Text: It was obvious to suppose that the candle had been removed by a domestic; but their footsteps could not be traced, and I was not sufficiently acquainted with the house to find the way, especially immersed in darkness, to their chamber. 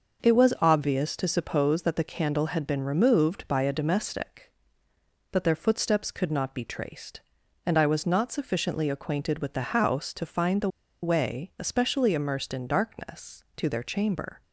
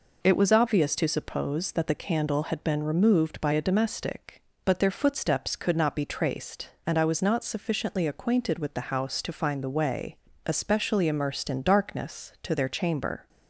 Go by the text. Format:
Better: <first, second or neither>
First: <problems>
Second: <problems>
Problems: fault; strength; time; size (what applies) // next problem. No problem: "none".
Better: second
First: starts louder than the rest; noticeable; until 1.3 s; 6 dB // pauses between "the" and "way"; slight; at 10.6 s; 0.35 s long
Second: none